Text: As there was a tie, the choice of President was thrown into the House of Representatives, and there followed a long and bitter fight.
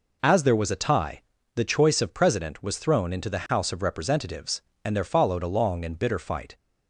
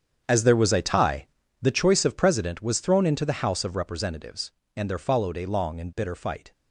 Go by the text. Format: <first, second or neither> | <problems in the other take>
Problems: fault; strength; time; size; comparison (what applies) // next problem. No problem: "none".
first | gets quieter; strong; throughout; 13.5 dB